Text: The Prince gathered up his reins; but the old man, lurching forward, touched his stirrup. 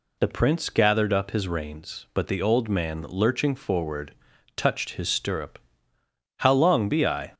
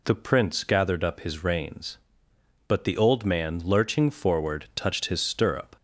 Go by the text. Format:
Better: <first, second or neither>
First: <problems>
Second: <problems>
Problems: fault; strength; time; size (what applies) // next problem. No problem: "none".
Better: second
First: goes on to say "How long be I"; noticeable; from 6.3 s on; 0.94 s long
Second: none